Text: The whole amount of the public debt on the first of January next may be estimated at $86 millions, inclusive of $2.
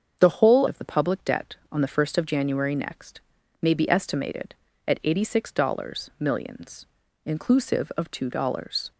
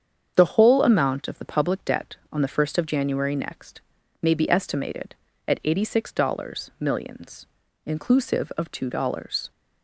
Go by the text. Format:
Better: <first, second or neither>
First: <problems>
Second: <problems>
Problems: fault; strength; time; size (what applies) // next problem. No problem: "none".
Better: second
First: starts louder than the rest; until 1.2 s; 7 dB // skips "amount"; at 0.6 s // pauses between "next" and "may"; at 3.2 s; 0.40 s long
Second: starts louder than the rest; strong; until 1.3 s; 7.5 dB // pauses between "next" and "may"; at 3.8 s; 0.40 s long